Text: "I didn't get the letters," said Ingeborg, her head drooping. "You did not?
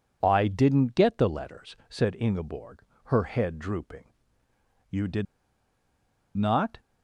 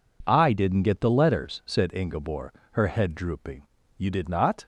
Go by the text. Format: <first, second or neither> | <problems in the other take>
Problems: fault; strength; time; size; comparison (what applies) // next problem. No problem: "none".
second | pauses between "did" and "not"; at 5.2 s; 1.1 s long